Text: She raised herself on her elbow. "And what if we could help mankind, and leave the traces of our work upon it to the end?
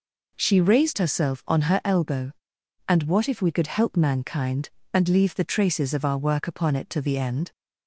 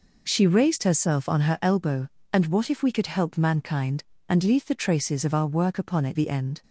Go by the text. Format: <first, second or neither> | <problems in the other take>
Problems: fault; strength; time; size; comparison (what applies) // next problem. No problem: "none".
first | skips "to"; at 6.1 s